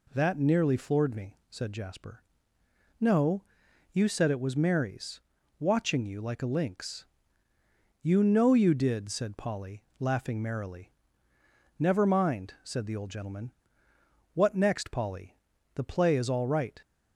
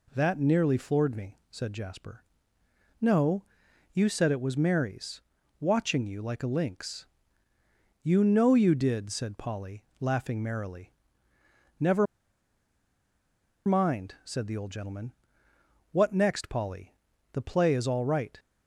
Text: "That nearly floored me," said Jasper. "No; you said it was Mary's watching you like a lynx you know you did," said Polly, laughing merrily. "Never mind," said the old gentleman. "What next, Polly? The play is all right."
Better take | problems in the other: first | pauses between "Mary's" and "watching"; at 5.2 s; 0.40 s long; also in the first // pauses between "lynx" and "you"; noticeable; at 7.0 s; 0.96 s long; noticeable in the first // pauses between "Never" and "mind"; strong; at 12.0 s; 1.6 s long

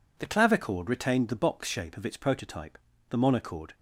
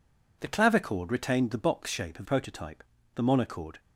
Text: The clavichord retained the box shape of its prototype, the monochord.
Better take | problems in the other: first | skips "its"; at 2.2 s

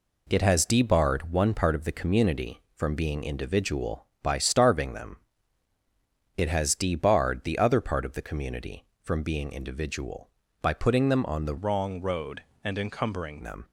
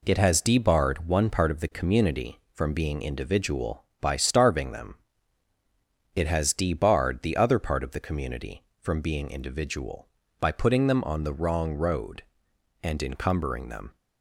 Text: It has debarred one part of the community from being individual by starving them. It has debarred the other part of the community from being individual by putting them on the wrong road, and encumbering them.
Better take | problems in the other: second | changes voice from "wrong" to "encumbering"; from 11.5 to 13.4 s; 1.9 s long

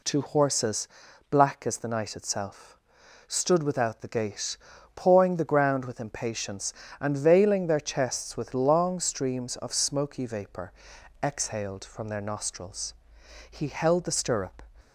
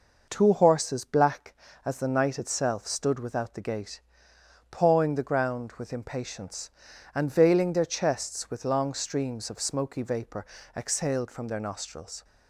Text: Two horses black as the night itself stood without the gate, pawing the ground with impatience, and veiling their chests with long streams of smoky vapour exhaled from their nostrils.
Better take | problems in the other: second | pauses between "horses" and "black"; at 0.8 s; 0.42 s long // pauses between "itself" and "stood"; noticeable; at 2.7 s; 0.52 s long // pauses between "vapour" and "exhaled"; noticeable; at 10.7 s; 0.50 s long; slight in the second // goes on to say "He held the stirrup"; noticeable; from 13.5 s on; 1.1 s long

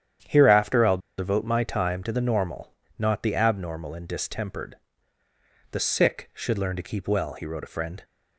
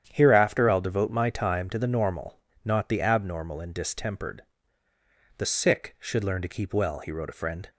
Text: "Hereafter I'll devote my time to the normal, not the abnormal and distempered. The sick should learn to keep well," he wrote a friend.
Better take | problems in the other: second | starts louder than the rest; strong; until 1.4 s; 9.5 dB; strong in the second // pauses between "I'll" and "devote"; slight; at 0.9 s; 0.19 s long

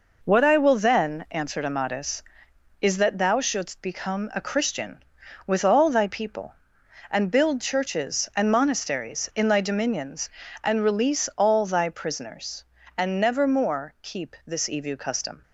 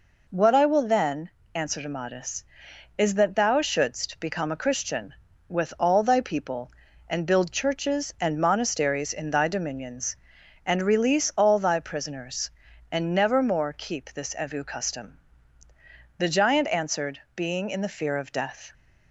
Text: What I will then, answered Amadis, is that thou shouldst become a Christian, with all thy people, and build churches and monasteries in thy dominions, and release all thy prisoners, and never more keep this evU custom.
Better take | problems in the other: first | goes on to say "The giant answered being in the fear of death"; strong; from 16.1 s on; 2.5 s long

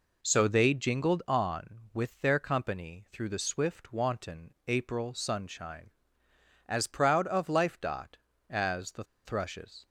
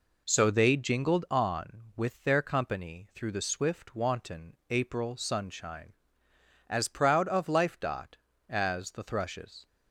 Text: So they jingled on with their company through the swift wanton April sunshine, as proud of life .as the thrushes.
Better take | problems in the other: second | pauses between "the" and "thrushes"; slight; at 9.0 s; 0.22 s long

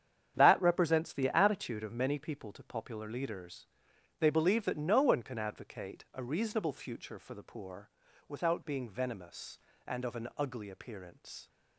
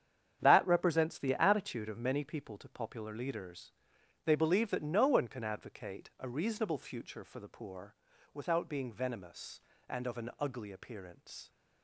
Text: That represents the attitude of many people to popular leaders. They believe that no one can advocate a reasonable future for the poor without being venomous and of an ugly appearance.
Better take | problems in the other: neither | starts louder than the rest; strong; the same in both // pauses between "poor" and "without"; the same in both

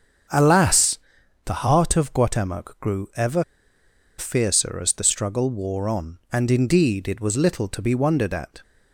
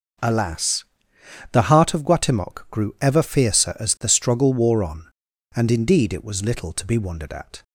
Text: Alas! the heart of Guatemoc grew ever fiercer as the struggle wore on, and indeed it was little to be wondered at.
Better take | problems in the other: second | starts louder than the rest; strong; until 1.7 s; 7.5 dB // pauses between "ever" and "fiercer"; noticeable; at 3.4 s; 0.75 s long

